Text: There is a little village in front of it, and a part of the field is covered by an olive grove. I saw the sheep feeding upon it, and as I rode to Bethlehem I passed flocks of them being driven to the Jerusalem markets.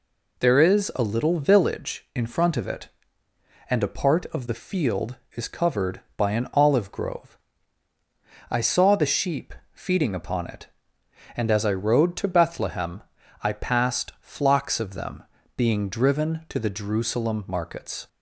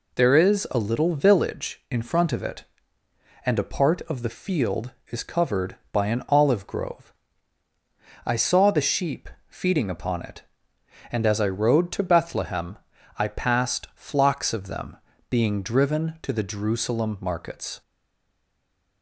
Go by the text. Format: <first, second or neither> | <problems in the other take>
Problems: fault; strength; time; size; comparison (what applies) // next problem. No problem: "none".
first | pauses between "sheep" and "feeding"; slight; at 9.2 s; 0.20 s long; slight in the first // pauses between "Bethlehem" and "I"; at 12.7 s; 0.42 s long; also in the first // pauses between "them" and "being"; slight; at 14.9 s; 0.32 s long; slight in the first // stays silent after the last word; noticeable; from 17.8 s on; 1.2 s long